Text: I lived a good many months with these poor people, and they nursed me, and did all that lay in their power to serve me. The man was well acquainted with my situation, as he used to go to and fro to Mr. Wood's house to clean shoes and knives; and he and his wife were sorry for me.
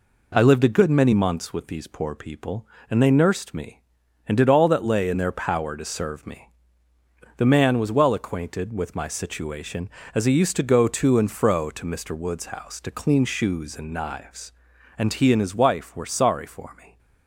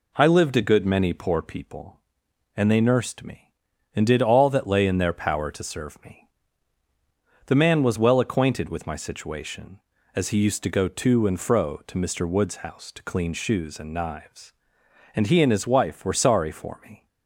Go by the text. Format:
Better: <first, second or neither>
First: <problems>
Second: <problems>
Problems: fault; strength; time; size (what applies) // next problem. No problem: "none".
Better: first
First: none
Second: skips "months with these"; at 1.1 s